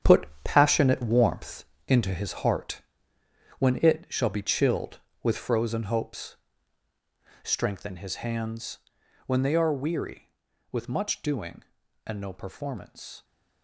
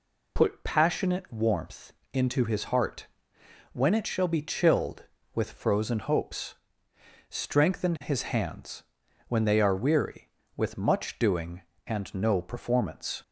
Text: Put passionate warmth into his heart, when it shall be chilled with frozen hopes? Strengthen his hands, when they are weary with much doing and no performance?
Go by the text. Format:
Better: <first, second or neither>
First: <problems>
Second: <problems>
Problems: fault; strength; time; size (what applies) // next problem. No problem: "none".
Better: second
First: gets quieter; strong; throughout; 10.5 dB // pauses between "Put" and "passionate"; slight; at 0.2 s; 0.16 s long // pauses between "warmth" and "into"; slight; at 1.6 s; 0.24 s long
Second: pauses between "warmth" and "into"; slight; at 1.9 s; 0.20 s long